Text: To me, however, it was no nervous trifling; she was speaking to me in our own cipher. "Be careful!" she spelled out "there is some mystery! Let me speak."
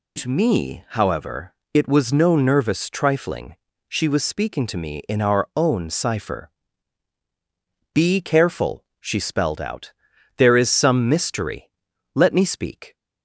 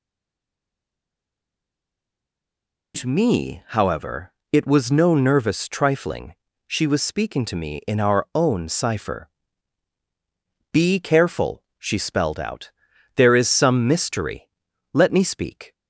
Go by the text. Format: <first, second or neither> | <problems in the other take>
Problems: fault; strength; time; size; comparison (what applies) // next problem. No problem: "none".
first | stays silent before the first word; strong; until 2.9 s; 2.9 s long // pauses between "out" and "there"; at 12.7 s; 0.44 s long; also in the first